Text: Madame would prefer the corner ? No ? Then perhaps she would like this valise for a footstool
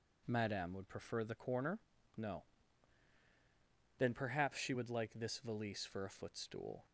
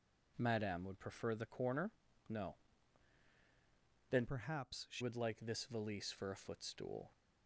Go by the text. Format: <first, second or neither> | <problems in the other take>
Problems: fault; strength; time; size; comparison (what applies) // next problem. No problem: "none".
first | changes voice from "perhaps" to "she"; from 4.2 to 5.0 s; 0.8 s long